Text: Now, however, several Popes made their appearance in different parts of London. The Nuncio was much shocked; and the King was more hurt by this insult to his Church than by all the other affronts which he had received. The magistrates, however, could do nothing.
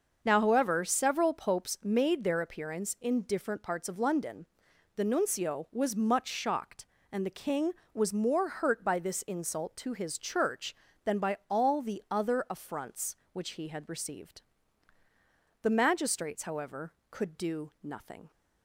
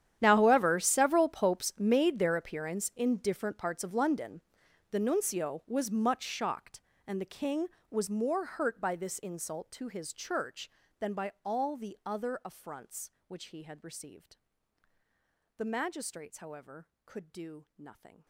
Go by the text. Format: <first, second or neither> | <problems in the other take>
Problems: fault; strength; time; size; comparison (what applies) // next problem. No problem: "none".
first | gets quieter; strong; throughout; 21.5 dB // starts louder than the rest; strong; until 1.2 s; 10 dB; also in the first